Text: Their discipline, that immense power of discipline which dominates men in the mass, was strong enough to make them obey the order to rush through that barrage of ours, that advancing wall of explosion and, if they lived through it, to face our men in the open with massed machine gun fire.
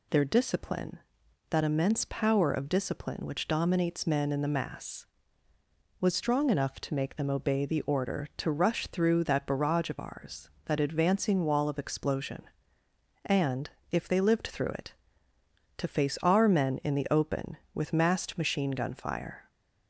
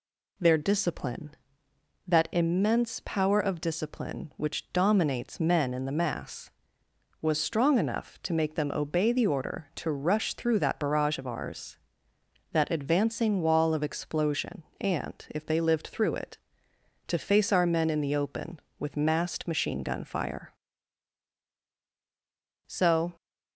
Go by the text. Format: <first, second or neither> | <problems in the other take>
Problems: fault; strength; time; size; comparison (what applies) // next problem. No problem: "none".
first | goes on to say "So"; slight; from 22.6 s on; 0.48 s long